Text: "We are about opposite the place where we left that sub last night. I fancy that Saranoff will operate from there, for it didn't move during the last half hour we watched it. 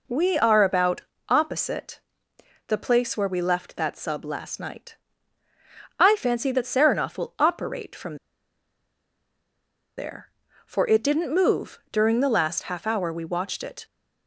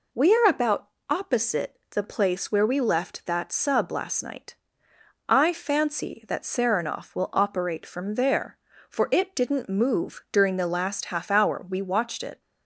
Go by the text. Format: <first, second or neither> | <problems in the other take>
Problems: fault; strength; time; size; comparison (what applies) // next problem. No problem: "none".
second | pauses between "about" and "opposite"; slight; at 1.0 s; 0.28 s long; slight in the second // pauses between "opposite" and "the"; noticeable; at 1.9 s; 0.68 s long // pauses between "from" and "there"; strong; at 8.1 s; 1.8 s long